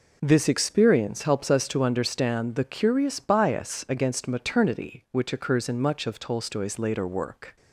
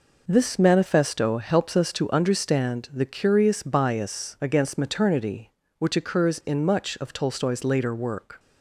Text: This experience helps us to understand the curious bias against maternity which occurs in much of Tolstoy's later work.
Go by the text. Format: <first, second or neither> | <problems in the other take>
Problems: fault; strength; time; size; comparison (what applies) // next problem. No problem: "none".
first | says "manifesto" for "experience"; at 0.5 s